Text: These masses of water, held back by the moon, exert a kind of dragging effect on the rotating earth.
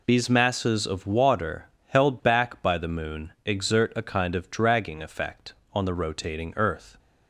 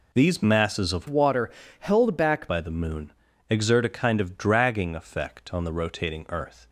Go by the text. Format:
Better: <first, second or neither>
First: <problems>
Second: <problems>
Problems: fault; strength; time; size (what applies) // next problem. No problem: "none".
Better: first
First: none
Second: changes voice from "water" to "back"; from 1.0 to 2.4 s; 1.4 s long